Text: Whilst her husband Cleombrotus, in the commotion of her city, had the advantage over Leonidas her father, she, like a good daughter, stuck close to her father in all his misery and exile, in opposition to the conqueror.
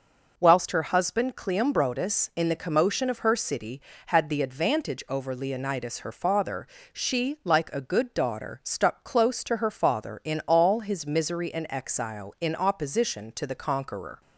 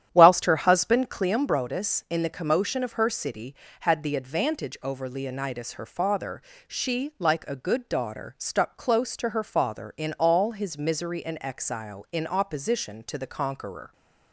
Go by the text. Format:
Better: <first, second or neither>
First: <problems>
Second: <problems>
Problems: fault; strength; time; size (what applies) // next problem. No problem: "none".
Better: first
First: none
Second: starts louder than the rest; strong; until 1.4 s; 10 dB